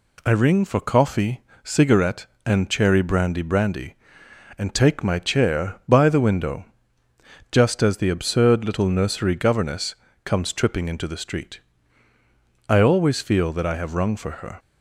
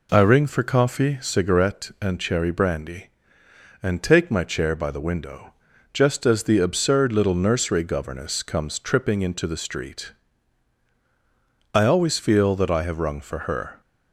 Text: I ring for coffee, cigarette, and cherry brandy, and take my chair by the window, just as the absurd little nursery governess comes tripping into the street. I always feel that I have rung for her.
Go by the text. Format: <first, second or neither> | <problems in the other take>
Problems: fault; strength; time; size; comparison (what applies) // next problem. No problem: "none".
second | says "brandy" twice; at 3.4 s // pauses between "governess" and "comes"; slight; at 9.9 s; 0.30 s long